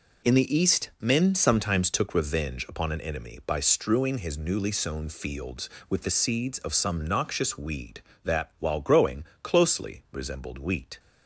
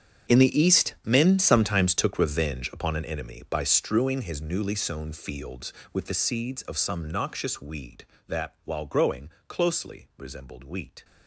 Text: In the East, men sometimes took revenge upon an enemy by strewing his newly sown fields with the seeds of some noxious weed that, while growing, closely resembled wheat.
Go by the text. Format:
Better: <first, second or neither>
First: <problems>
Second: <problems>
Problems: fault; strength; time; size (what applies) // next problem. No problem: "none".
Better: first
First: none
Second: gets quieter; strong; throughout; 17 dB